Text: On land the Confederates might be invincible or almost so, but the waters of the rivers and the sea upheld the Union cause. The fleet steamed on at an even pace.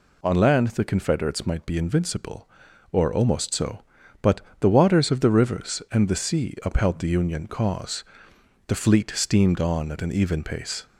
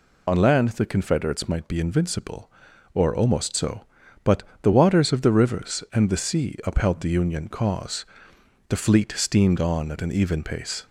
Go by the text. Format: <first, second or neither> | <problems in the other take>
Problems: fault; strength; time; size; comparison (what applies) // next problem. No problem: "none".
first | loses the start of "On"; at 0.2 s; 35 ms // pauses between "but" and "the"; slight; at 4.4 s; 0.20 s long; slight in the first